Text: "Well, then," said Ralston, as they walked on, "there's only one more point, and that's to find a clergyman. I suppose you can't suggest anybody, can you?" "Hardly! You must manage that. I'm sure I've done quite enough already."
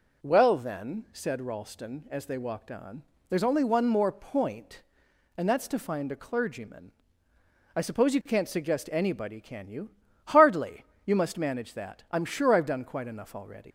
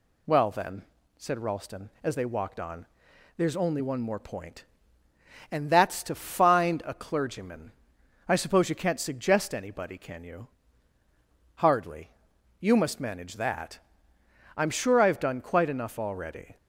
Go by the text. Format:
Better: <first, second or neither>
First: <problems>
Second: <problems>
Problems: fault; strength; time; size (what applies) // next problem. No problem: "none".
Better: second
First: leaves "already" unfinished; at 13.6 s; 120 ms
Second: none